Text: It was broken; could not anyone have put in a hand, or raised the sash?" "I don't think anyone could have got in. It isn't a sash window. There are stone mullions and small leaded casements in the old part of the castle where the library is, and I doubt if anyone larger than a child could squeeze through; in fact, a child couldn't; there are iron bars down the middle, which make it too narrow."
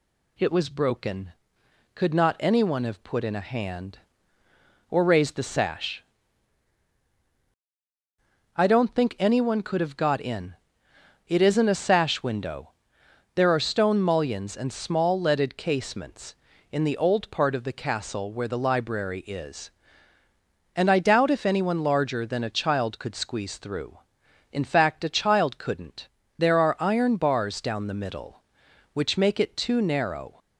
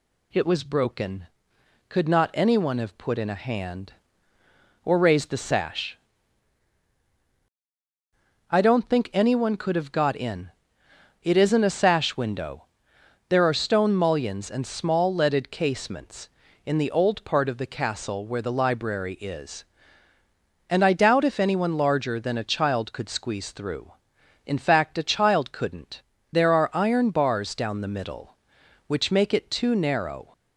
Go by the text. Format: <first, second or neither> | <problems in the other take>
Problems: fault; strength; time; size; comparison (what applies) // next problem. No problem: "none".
neither | none